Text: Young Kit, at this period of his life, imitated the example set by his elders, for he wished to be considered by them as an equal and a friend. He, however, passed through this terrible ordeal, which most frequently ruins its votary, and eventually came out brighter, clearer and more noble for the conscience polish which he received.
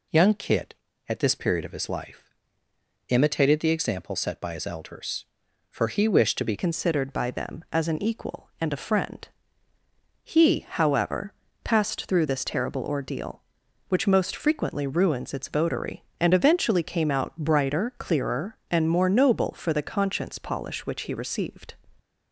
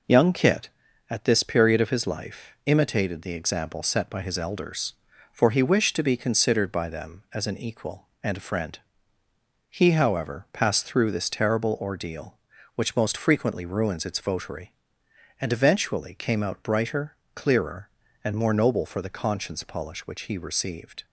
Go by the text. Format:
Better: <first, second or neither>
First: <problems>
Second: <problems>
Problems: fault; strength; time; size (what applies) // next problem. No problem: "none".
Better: second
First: changes voice at "considered"; from 6.5 s on; 15.2 s long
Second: none